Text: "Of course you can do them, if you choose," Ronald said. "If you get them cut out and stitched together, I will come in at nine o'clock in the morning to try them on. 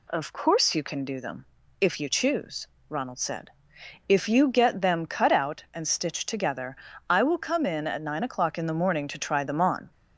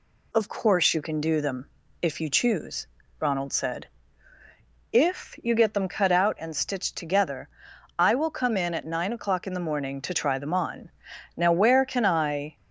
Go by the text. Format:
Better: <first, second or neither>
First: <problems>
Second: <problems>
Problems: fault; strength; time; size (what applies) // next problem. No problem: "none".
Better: first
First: none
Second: goes on to say "Now where can I"; noticeable; from 11.3 s on; 1.2 s long